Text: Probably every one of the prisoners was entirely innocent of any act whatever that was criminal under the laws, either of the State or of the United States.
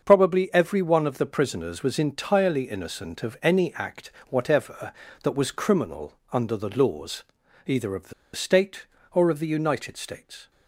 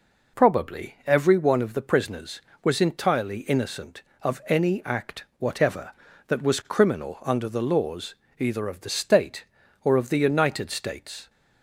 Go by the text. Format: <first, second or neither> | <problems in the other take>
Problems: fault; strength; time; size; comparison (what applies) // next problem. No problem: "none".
second | starts louder than the rest; until 1.0 s; 6.5 dB // pauses between "act" and "whatever"; slight; at 4.1 s; 0.18 s long // pauses between "criminal" and "under"; slight; at 6.1 s; 0.18 s long // pauses between "the" and "State"; slight; at 8.1 s; 0.22 s long